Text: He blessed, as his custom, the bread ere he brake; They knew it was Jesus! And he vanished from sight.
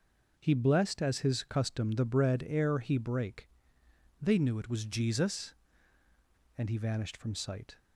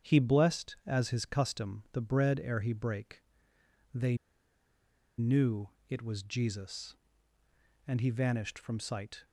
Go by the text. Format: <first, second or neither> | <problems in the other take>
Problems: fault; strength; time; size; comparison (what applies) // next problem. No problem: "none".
first | starts louder than the rest; strong; until 1.1 s; 8 dB // pauses between "They" and "knew"; at 4.1 s; 1.0 s long // pauses between "knew" and "it"; slight; at 5.6 s; 0.22 s long